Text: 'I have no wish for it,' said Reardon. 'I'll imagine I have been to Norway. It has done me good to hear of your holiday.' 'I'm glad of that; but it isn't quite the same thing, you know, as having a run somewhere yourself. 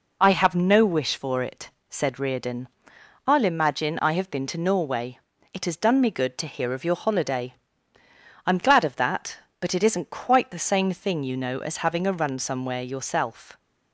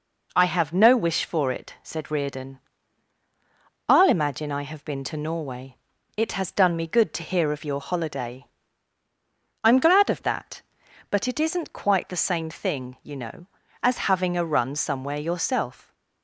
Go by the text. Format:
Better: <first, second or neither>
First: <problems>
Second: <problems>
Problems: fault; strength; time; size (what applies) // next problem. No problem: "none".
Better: neither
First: none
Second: none